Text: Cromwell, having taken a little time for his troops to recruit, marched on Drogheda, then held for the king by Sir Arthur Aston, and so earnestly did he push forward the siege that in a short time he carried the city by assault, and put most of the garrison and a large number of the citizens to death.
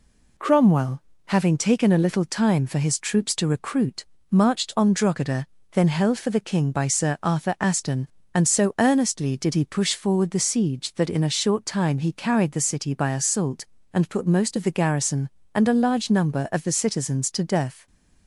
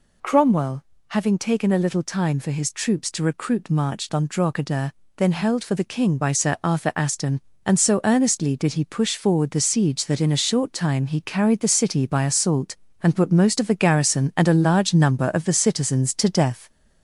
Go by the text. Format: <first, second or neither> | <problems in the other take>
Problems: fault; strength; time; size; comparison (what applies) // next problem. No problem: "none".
first | gets louder; throughout; 3.5 dB